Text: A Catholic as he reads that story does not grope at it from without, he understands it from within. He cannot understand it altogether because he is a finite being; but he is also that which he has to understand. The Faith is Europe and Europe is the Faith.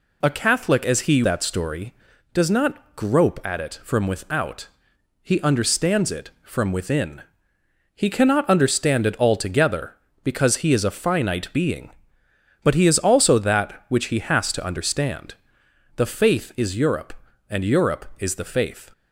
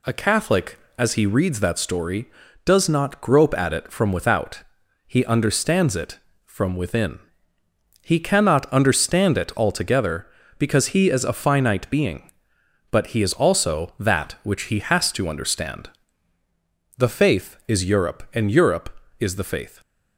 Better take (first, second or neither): second